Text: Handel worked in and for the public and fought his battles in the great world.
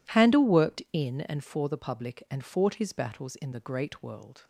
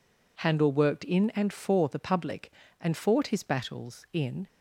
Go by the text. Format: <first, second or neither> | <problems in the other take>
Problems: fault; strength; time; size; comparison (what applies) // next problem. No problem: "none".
first | stops before "the great world"; at 4.4 s